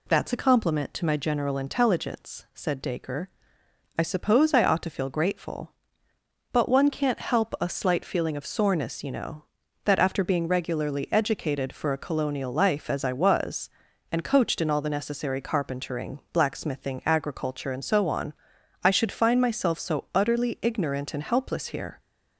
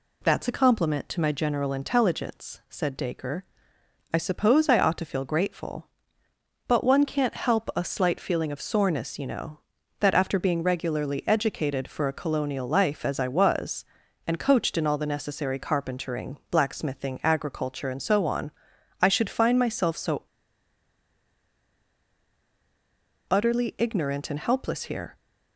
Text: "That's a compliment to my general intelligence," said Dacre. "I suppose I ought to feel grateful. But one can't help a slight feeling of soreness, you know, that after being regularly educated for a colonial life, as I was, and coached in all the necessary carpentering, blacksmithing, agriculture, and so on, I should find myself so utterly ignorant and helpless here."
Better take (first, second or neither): first